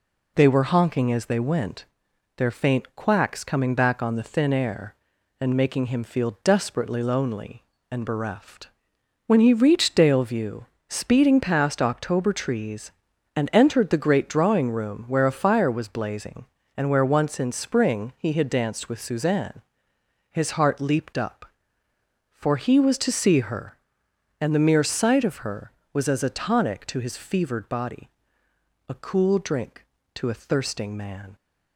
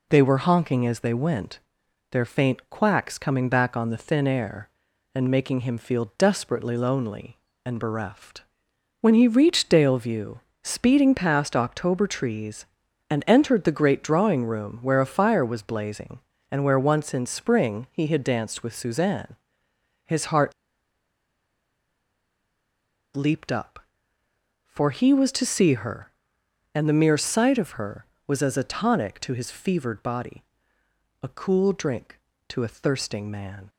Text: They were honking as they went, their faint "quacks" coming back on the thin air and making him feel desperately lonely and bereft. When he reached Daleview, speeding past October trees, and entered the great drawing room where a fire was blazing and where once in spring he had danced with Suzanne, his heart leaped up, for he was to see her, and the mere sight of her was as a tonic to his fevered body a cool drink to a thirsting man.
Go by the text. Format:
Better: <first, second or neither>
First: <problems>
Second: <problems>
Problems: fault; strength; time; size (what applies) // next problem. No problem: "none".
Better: first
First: pauses between "body" and "a"; noticeable; at 28.0 s; 0.78 s long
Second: pauses between "heart" and "leaped"; strong; at 20.5 s; 2.6 s long // pauses between "body" and "a"; noticeable; at 30.4 s; 0.78 s long